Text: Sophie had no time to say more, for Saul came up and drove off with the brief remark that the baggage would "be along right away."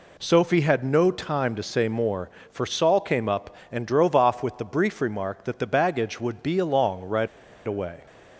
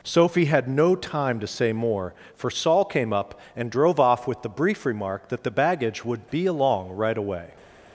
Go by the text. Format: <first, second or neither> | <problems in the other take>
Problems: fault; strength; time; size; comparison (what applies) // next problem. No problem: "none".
second | pauses between "right" and "away"; at 7.2 s; 0.39 s long